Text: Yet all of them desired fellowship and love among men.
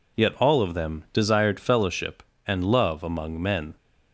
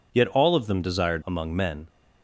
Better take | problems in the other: first | skips "fellowship and love"; at 1.2 s

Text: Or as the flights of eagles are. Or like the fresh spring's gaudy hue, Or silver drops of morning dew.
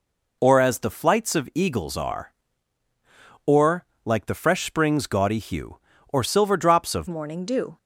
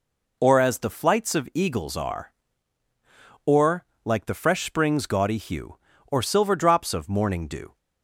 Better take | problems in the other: second | pauses between "Or" and "like"; slight; at 3.8 s; 0.20 s long; slight in the second // changes voice at "morning"; from 7.0 s on; 0.7 s long

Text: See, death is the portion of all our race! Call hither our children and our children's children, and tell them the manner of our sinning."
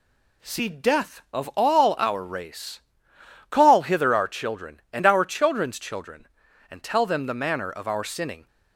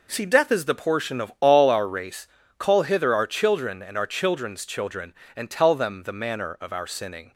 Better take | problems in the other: second | skips "is the portion"; at 1.2 s

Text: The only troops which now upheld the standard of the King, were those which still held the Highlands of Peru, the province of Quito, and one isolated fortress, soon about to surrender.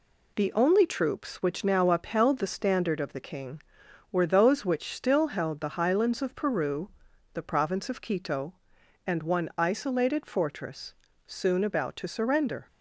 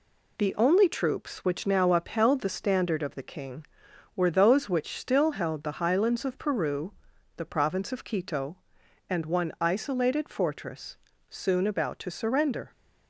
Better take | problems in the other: neither | none

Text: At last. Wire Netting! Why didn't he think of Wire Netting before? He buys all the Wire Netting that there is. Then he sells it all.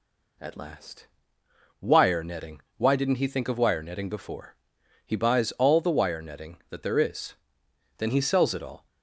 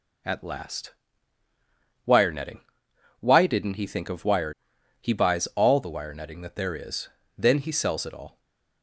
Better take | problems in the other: first | skips "Netting before"; at 4.7 s // stays silent after the last word; slight; from 8.2 s on; 0.6 s long

